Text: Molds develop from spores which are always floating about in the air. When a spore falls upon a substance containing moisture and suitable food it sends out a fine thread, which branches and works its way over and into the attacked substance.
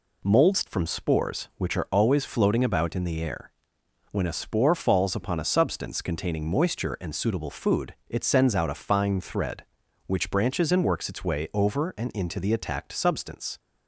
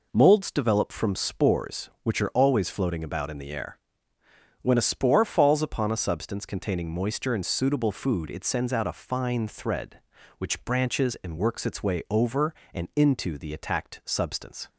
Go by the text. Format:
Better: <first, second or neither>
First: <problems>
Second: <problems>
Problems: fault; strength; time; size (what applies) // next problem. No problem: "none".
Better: second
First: skips "develop"; at 0.6 s // pauses between "food" and "it"; slight; at 7.9 s; 0.16 s long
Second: none